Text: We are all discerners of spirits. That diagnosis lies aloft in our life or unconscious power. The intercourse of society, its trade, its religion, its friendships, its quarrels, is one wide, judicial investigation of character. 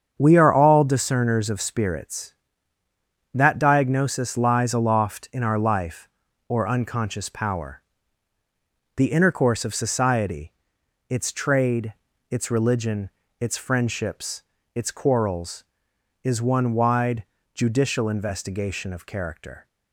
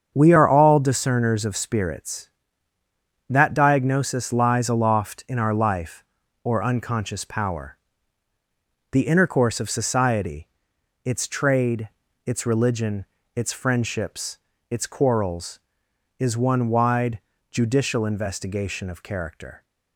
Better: neither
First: starts louder than the rest; strong; until 1.1 s; 7.5 dB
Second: starts louder than the rest; strong; until 1.1 s; 7.5 dB

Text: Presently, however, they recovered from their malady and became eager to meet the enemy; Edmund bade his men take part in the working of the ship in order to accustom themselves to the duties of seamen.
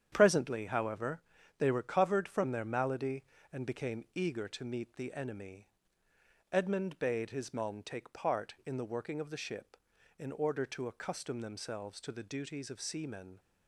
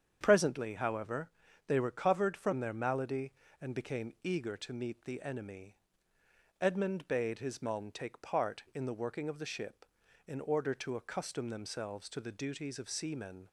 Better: second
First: gets quieter; strong; throughout; 7.5 dB // starts louder than the rest; strong; until 1.1 s; 9 dB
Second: starts louder than the rest; strong; until 1.2 s; 8 dB

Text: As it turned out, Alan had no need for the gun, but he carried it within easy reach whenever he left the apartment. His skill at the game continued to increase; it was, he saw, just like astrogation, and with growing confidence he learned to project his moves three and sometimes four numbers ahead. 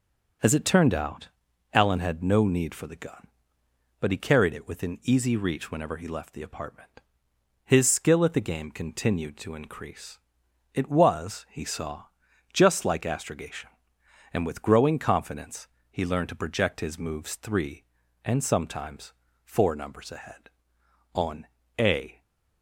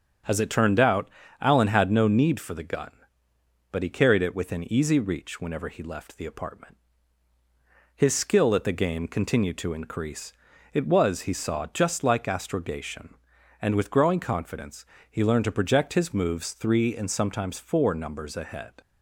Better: second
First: starts louder than the rest; until 1.8 s; 6.5 dB // pauses between "confidence" and "he"; slight; at 15.6 s; 0.22 s long // pauses between "sometimes" and "four"; slight; at 19.1 s; 0.30 s long // goes on to say "On a"; noticeable; from 21.1 s on; 1.0 s long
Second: starts louder than the rest; until 1.5 s; 6.5 dB // pauses between "confidence" and "he"; slight; at 14.8 s; 0.24 s long

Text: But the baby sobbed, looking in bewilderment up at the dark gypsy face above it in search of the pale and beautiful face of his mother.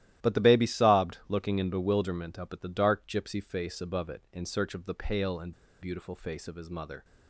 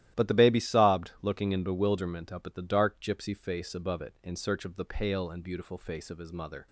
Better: second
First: starts louder than the rest; strong; until 1.3 s; 13.5 dB // pauses between "and" and "beautiful"; slight; at 5.5 s; 0.29 s long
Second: starts louder than the rest; strong; until 1.2 s; 13.5 dB

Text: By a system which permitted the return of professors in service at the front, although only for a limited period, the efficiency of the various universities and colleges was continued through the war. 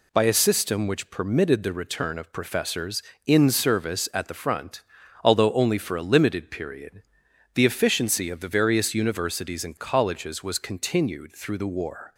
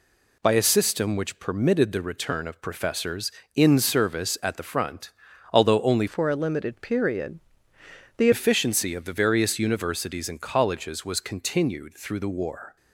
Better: first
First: none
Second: changes voice from "for" to "the"; from 6.0 to 8.2 s; 2.2 s long

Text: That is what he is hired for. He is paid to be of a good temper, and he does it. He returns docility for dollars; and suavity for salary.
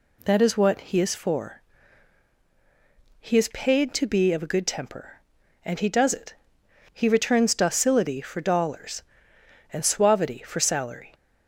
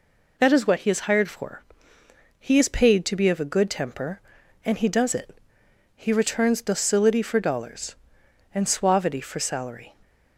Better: second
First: skips "hired"; at 1.1 s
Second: none

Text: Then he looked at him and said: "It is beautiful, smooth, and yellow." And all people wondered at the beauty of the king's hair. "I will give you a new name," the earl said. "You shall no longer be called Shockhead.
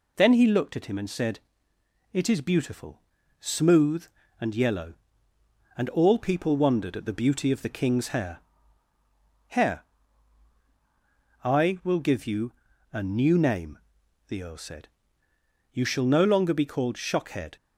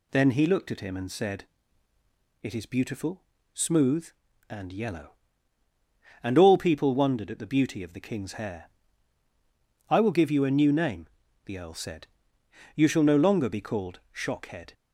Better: second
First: says "hair" twice; at 9.4 s // pauses between "you" and "a"; at 12.5 s; 0.40 s long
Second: none

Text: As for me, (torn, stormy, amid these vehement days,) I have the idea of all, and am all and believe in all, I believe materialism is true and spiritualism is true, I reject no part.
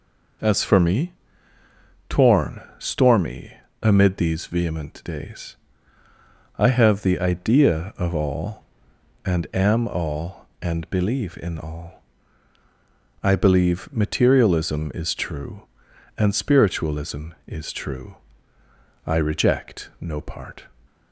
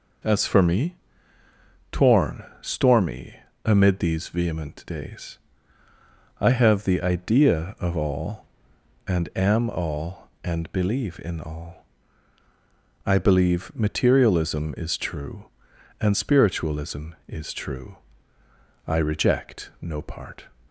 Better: neither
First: none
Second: none

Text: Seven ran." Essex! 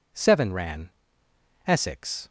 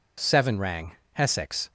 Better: first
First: none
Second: says "rang" for "ran"; at 0.5 s

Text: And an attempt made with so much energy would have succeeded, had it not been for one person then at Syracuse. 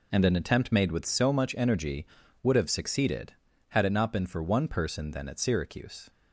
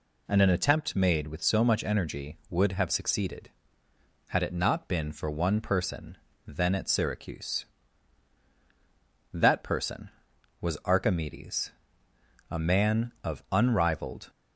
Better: first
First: none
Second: pauses between "person" and "then"; slight; at 6.1 s; 0.30 s long // goes on to say "That person was Archimedes a man of unrivaled"; strong; from 9.3 s on; 4.9 s long

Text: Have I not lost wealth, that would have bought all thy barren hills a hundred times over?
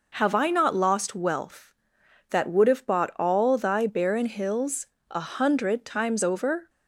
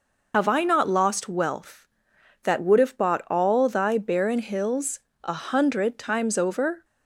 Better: first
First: pauses between "hills" and "a"; slight; at 4.8 s; 0.22 s long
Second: loses the start of "Have"; at 0.3 s; 90 ms // pauses between "hills" and "a"; slight; at 5.0 s; 0.22 s long

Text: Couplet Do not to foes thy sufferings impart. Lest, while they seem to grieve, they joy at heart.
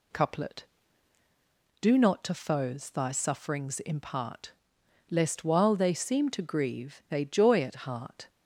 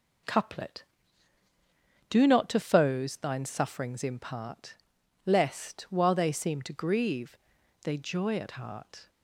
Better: first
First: none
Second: says "thine" for "thy"; at 3.1 s

